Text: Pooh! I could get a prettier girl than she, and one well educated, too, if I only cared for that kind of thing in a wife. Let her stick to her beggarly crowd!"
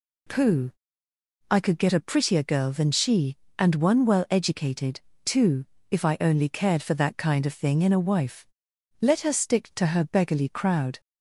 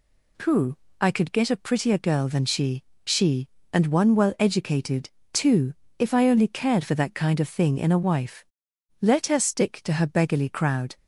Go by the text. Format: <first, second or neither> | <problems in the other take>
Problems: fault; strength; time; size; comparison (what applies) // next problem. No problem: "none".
first | says "she" twice; at 3.0 s